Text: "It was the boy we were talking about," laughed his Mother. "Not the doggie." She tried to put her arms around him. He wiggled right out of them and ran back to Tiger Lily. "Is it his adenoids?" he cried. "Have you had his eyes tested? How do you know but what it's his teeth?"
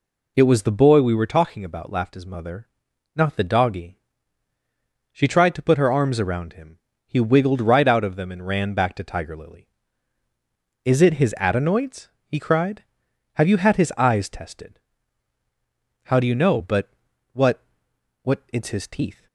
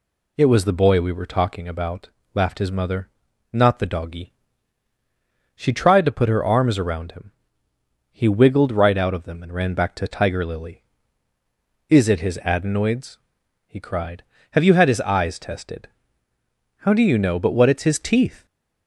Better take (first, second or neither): second